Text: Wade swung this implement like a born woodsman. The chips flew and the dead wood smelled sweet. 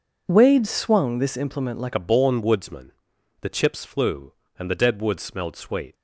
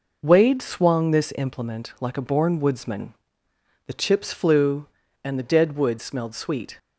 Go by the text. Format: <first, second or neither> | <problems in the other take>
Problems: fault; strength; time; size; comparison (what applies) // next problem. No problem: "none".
second | changes voice at "a"; from 1.9 s on; 4.0 s long